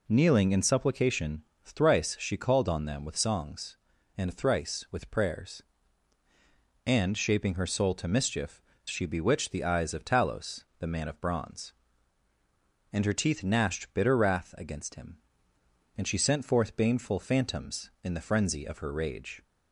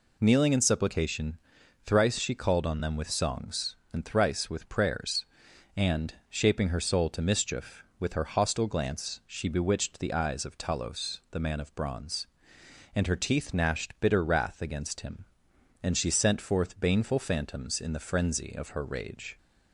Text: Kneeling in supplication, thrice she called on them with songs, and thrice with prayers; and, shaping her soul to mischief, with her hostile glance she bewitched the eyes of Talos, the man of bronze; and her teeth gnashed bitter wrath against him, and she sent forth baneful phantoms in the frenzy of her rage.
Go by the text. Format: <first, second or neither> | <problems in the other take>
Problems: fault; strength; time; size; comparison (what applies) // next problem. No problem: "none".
second | skips "with her hostile glance"; at 8.7 s